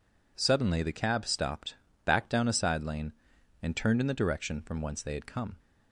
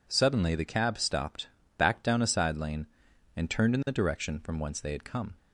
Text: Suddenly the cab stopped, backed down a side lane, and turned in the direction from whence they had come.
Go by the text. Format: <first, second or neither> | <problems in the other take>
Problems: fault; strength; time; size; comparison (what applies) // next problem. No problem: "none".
neither | none